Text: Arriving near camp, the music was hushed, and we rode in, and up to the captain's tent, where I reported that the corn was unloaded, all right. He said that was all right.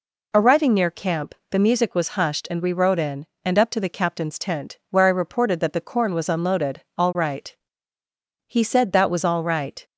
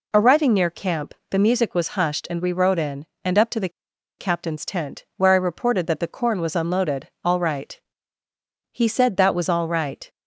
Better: first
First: none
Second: pauses between "the" and "captain's"; noticeable; at 3.6 s; 0.49 s long

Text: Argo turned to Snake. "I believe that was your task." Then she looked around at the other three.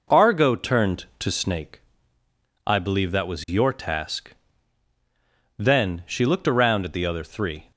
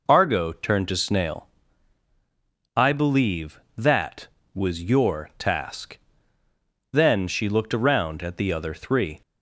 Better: first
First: none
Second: says "Snail" for "Snake"; at 0.9 s

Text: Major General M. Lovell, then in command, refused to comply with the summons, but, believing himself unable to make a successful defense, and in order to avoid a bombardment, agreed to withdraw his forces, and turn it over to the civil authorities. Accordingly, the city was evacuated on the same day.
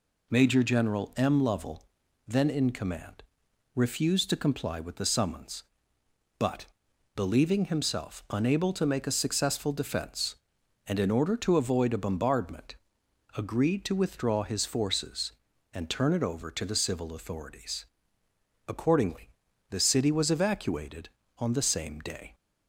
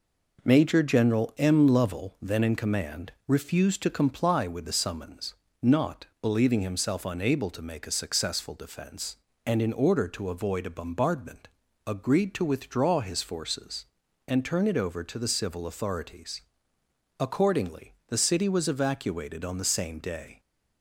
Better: first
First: none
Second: says "not" for "but"; at 5.6 s

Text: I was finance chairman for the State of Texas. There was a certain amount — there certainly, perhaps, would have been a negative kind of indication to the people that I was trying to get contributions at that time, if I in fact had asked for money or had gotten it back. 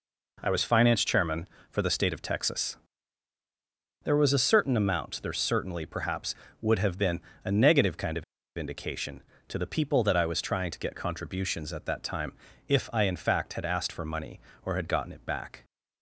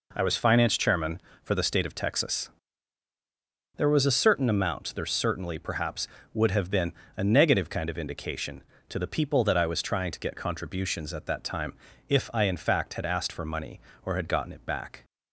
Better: second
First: pauses between "been" and "a"; slight; at 7.1 s; 0.24 s long // pauses between "of" and "indication"; slight; at 8.2 s; 0.32 s long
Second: pauses between "been" and "a"; slight; at 6.9 s; 0.24 s long

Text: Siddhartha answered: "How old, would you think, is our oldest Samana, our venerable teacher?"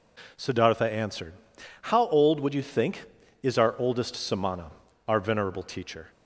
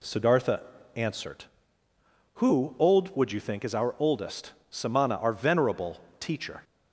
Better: first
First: none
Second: pauses between "Siddhartha" and "answered"; slight; at 0.6 s; 0.34 s long // says "Who" for "How"; at 2.3 s // pauses between "oldest" and "Samana"; slight; at 4.5 s; 0.18 s long // pauses between "venerable" and "teacher"; slight; at 6.0 s; 0.18 s long

